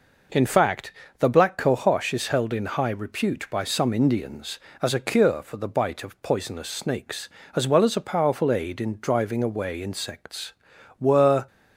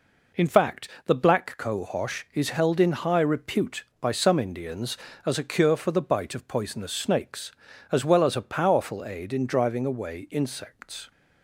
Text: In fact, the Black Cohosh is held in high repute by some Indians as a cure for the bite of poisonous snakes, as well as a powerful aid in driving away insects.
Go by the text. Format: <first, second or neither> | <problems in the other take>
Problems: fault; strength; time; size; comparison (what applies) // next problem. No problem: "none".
second | goes on to say "Were"; slight; from 10.9 s on; 0.48 s long